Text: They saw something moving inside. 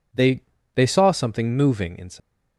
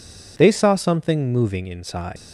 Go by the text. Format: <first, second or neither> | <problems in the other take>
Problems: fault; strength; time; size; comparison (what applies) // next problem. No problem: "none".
second | says "They" twice; at 0.7 s